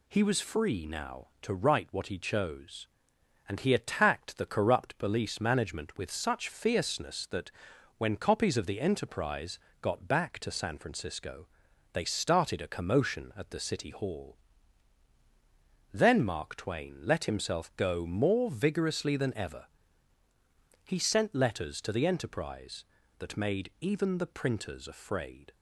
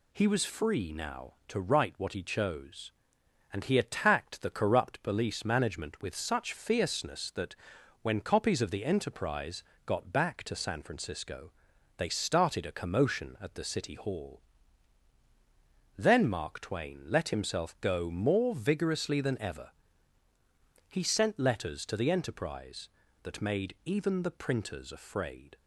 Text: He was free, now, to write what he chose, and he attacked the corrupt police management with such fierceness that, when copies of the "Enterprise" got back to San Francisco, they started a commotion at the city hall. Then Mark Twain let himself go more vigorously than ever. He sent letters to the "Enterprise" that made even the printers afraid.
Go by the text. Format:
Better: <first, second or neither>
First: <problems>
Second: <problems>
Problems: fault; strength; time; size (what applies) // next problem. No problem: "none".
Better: neither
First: pauses between "Enterprise" and "got"; slight; at 9.5 s; 0.22 s long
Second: pauses between "Enterprise" and "got"; slight; at 9.6 s; 0.22 s long